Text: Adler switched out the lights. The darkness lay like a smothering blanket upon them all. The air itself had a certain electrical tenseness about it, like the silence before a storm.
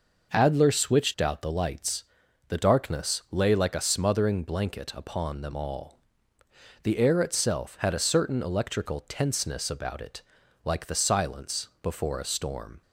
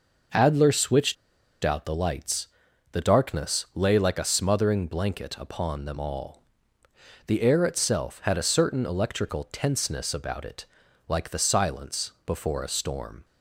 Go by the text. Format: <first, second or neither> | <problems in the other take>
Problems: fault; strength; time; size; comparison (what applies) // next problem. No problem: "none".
first | pauses between "switched" and "out"; noticeable; at 1.1 s; 0.47 s long